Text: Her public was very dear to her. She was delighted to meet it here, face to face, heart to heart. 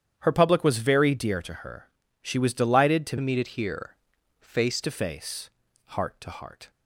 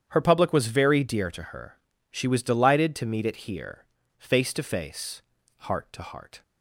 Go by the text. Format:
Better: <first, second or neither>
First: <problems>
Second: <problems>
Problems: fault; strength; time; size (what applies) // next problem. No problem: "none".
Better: second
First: starts louder than the rest; strong; until 1.2 s; 9.5 dB // changes voice from "meet" to "face"; from 3.2 to 4.8 s; 1.6 s long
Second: starts louder than the rest; strong; until 1.0 s; 9 dB